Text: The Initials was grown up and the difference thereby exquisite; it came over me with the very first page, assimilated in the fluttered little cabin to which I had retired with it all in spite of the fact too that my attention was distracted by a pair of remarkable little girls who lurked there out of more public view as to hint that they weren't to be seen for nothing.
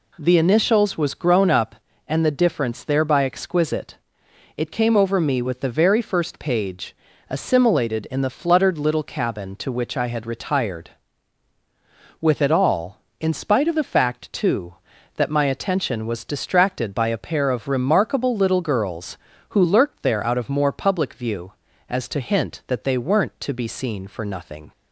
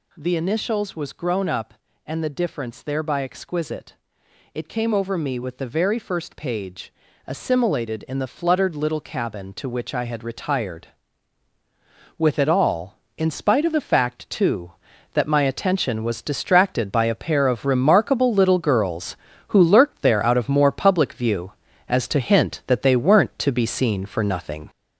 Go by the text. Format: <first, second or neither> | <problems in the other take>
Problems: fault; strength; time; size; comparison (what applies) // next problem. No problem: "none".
first | gets louder; noticeable; throughout; 5.5 dB